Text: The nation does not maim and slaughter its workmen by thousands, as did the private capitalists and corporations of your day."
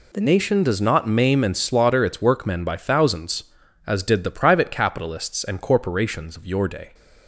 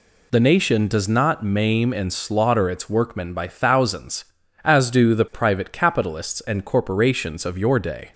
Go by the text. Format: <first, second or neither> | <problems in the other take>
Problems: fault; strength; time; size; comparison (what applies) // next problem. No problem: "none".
first | says "do" for "did"; at 4.8 s